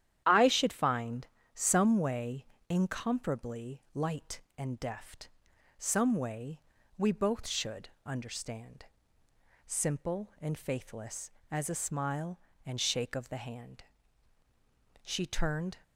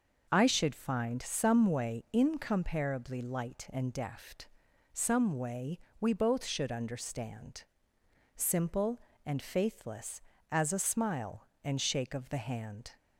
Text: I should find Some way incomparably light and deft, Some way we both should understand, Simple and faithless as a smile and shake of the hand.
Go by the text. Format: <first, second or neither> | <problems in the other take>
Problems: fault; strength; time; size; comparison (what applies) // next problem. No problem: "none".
second | starts louder than the rest; strong; until 1.2 s; 10.5 dB // pauses between "find" and "Some"; slight; at 1.2 s; 0.26 s long // pauses between "way" and "incomparably"; slight; at 2.4 s; 0.24 s long // pauses between "way" and "we"; at 6.5 s; 0.38 s long; slight in the second // pauses between "should" and "understand"; slight; at 7.8 s; 0.18 s long // goes on to say "She turned"; noticeable; from 15.0 s on; 0.76 s long